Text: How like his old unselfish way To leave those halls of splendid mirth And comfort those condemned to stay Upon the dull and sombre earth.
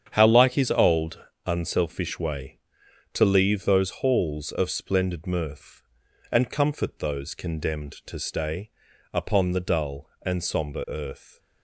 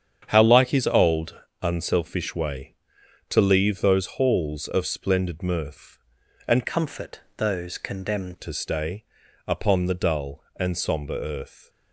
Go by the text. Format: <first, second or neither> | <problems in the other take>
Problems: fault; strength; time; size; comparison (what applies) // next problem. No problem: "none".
first | starts louder than the rest; strong; until 1.2 s; 8 dB; strong in the first // pauses between "old" and "unselfish"; slight; at 1.3 s; 0.24 s long; slight in the first // changes voice from "comfort" to "condemned"; from 6.6 to 8.3 s; 1.7 s long // pauses between "comfort" and "those"; slight; at 7.2 s; 0.16 s long // pauses between "stay" and "Upon"; at 9.0 s; 0.42 s long; also in the first